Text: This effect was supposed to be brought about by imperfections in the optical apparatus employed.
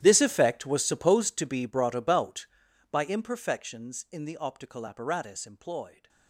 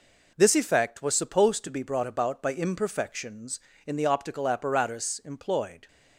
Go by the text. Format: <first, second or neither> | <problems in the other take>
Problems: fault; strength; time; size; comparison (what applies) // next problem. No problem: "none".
second | gets quieter; strong; throughout; 19.5 dB